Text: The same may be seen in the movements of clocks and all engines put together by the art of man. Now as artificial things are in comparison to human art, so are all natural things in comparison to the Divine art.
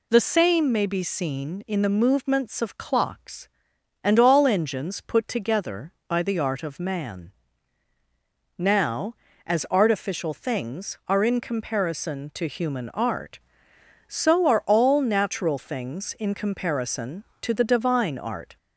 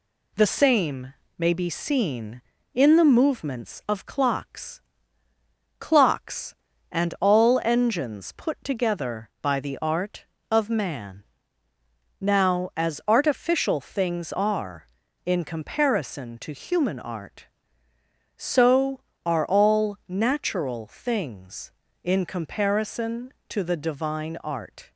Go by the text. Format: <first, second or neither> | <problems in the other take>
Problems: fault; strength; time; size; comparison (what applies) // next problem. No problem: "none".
first | pauses between "same" and "may"; slight; at 1.1 s; 0.24 s long // says "clocks" twice; at 5.7 s